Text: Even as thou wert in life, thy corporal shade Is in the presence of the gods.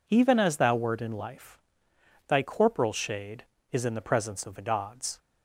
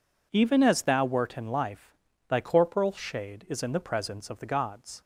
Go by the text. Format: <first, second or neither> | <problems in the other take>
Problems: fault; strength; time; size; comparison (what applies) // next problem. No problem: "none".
neither | none